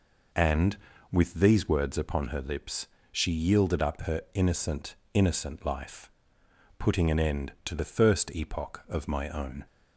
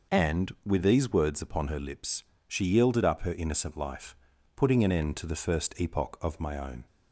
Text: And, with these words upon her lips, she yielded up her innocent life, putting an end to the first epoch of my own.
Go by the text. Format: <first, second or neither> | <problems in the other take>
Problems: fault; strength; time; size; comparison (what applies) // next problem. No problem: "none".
second | says "innocent" twice; at 5.1 s